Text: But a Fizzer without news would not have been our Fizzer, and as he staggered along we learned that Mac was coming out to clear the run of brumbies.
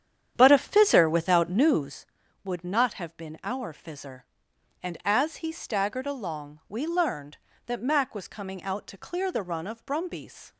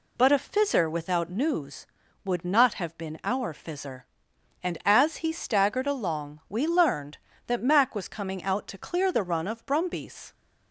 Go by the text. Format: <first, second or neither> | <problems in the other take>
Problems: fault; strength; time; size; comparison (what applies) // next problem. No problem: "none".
second | starts louder than the rest; strong; until 2.0 s; 9.5 dB